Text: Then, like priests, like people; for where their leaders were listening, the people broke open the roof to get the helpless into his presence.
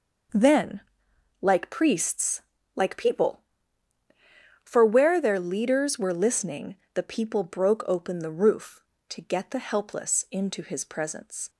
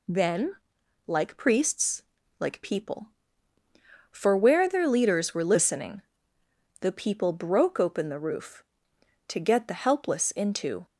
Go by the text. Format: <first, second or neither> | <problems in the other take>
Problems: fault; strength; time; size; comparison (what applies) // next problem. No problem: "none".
first | stops before "his presence"; at 10.8 s